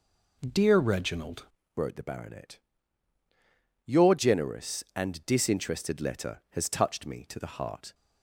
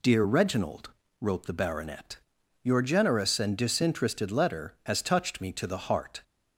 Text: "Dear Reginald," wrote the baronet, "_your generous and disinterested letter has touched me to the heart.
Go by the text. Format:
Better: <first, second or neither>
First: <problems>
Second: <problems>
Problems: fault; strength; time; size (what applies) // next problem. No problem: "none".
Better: second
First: changes voice at "wrote"; from 1.7 s on; 6.2 s long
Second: none